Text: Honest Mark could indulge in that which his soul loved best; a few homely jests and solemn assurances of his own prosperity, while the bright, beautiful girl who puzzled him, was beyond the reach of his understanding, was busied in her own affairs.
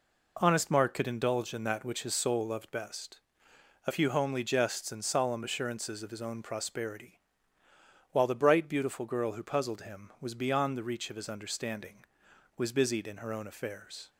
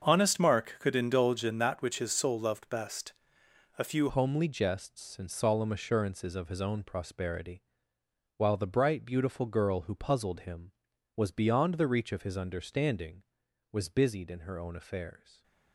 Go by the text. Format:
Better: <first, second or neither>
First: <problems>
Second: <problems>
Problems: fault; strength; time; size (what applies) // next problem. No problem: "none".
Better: first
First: none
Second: starts louder than the rest; until 1.1 s; 7 dB // changes voice at "homely"; from 4.0 s on; 11.4 s long